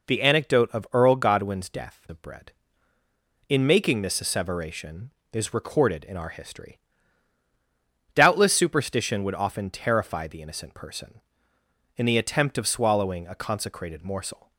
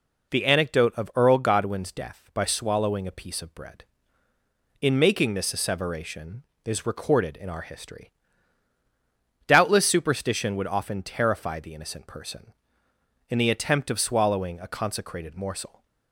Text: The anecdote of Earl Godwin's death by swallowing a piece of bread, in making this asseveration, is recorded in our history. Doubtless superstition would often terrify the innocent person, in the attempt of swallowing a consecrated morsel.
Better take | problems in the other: second | skips "by swallowing a piece"; at 2.0 s

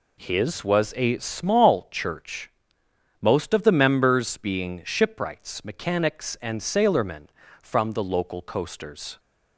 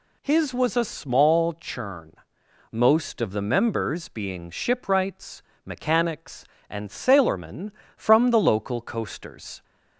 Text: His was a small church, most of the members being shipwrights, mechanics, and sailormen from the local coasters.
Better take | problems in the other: first | says "churn" for "church"; at 1.5 s

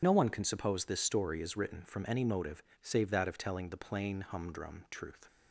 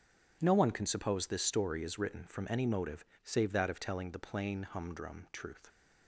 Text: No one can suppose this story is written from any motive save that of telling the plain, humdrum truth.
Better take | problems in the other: second | loses the start of "No"; at 0.0 s; 45 ms // pauses between "motive" and "save"; slight; at 2.6 s; 0.20 s long; slight in the second

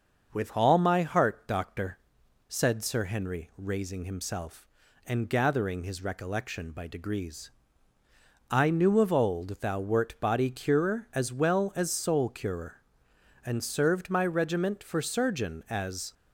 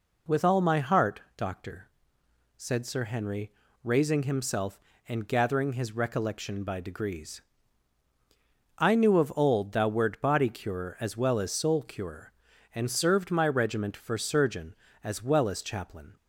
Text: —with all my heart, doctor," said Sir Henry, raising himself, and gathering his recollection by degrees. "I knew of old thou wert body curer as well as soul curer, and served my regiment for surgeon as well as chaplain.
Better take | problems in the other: second | starts louder than the rest; until 1.3 s; 6.5 dB // stops before "well as chaplain"; at 16.1 s

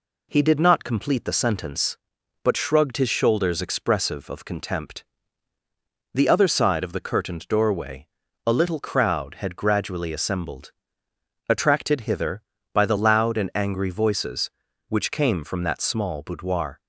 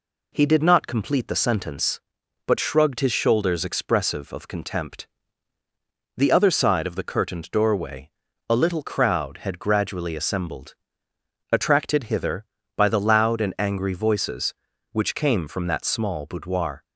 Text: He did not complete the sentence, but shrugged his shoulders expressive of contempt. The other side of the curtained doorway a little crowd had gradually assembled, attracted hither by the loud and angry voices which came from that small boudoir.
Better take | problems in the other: neither | pauses between "doorway" and "a"; the same in both

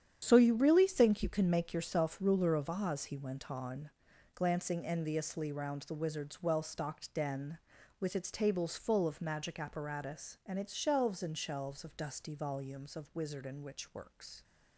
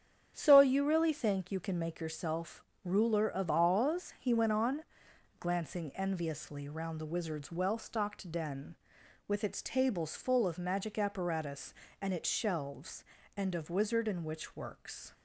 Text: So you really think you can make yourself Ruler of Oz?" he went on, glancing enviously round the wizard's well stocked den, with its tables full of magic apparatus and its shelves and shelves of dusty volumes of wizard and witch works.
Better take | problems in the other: first | starts louder than the rest; strong; until 1.3 s; 8 dB; strong in the first // pauses between "yourself" and "Ruler"; slight; at 2.6 s; 0.22 s long // skips "shelves of dusty volumes"; at 13.5 s

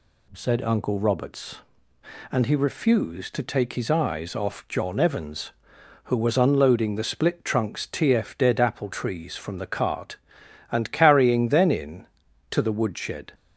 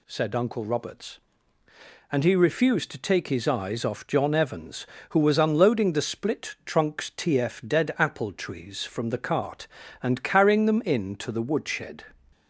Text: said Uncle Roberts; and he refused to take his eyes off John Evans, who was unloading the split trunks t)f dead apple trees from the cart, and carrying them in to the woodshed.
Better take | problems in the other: second | says "then" for "them"; at 11.4 s

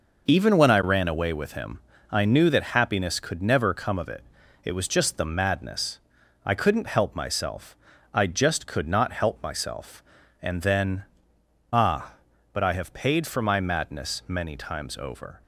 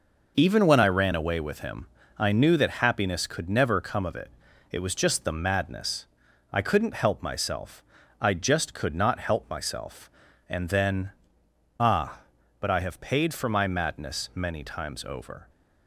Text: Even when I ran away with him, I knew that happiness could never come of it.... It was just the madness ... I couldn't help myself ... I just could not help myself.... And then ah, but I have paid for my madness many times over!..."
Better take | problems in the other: neither | pauses between "then" and "ah"; noticeable; the same in both

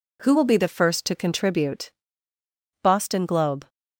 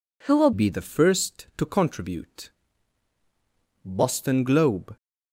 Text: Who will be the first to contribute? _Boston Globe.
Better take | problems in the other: first | changes voice at "be"; from 0.5 s on; 4.4 s long

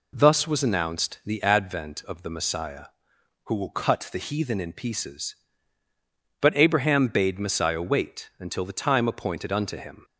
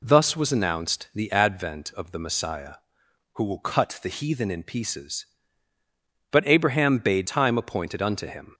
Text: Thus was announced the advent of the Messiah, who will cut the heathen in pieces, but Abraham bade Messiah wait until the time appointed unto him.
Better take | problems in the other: first | skips "Messiah wait until the"; at 7.2 s

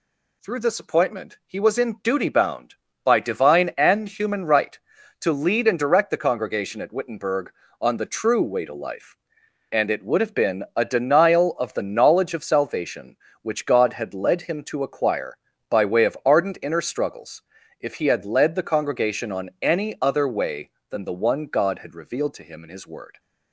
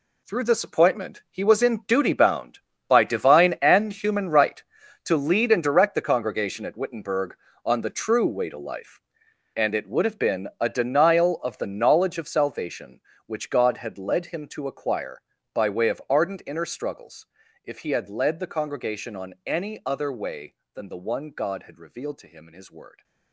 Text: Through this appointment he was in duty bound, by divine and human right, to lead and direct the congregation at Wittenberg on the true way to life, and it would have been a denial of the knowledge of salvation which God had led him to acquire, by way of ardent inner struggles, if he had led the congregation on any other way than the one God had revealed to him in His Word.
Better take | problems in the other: first | gets quieter; strong; throughout; 11 dB

